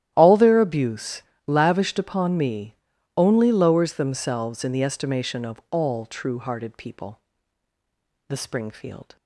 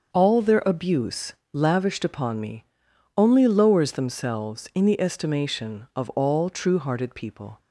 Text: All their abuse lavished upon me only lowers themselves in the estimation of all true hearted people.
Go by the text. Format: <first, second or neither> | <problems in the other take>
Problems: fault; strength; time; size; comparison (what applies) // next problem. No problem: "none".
second | starts louder than the rest; strong; until 1.1 s; 12 dB; also in the second // pauses between "abuse" and "lavished"; slight; at 1.2 s; 0.24 s long; slight in the second // pauses between "me" and "only"; at 2.7 s; 0.42 s long; noticeable in the second // goes on to say "The Springfield"; noticeable; from 8.2 s on; 0.88 s long